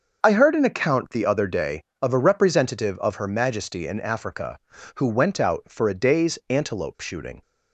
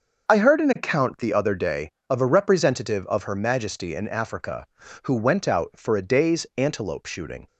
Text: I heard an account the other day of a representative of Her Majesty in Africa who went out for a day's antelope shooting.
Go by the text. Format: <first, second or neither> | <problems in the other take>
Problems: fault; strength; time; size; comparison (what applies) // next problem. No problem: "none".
neither | starts louder than the rest; the same in both